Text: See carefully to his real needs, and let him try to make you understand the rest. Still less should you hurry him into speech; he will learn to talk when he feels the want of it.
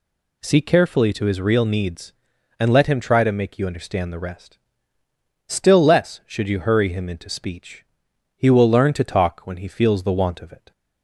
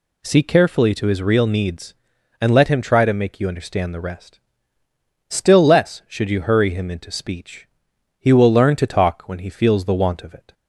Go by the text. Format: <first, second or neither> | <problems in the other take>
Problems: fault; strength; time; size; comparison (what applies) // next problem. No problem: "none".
neither | none